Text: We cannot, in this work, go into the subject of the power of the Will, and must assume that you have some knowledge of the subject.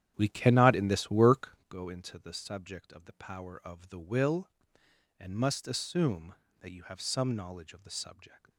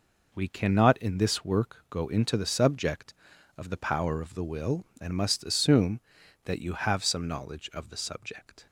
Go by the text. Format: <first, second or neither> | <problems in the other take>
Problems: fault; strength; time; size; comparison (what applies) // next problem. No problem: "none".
second | starts louder than the rest; strong; until 1.8 s; 10 dB